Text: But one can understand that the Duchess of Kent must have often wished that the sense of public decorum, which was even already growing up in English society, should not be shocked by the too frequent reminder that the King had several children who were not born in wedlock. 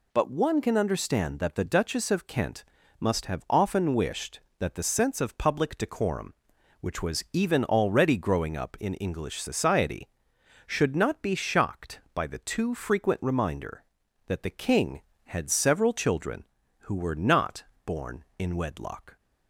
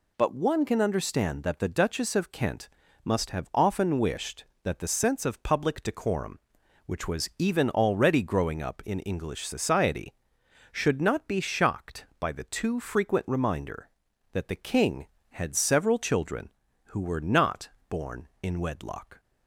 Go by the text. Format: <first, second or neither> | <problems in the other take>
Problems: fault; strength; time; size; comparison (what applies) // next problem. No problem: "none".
neither | pauses between "Kent" and "must"; slight; the same in both // pauses between "not" and "born"; slight; the same in both